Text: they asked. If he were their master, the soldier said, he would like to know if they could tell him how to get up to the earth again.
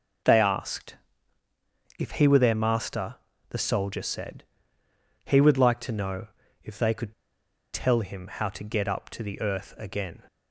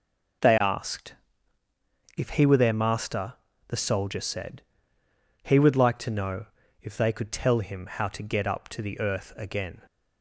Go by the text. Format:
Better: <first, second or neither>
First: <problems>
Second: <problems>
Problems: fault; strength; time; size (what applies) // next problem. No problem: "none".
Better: second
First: pauses between "know" and "if"; slight; at 6.2 s; 0.36 s long // pauses between "could" and "tell"; noticeable; at 7.1 s; 0.60 s long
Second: pauses between "know" and "if"; slight; at 6.4 s; 0.36 s long